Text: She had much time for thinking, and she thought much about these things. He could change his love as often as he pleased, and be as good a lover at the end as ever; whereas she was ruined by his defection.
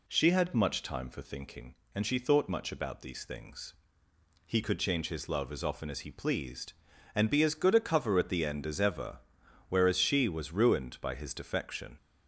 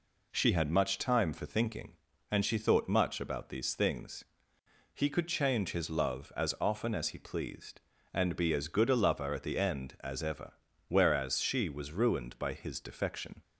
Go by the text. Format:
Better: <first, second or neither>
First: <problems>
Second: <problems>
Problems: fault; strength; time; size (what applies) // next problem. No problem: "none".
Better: second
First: says "cover" for "lover"; at 7.8 s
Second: none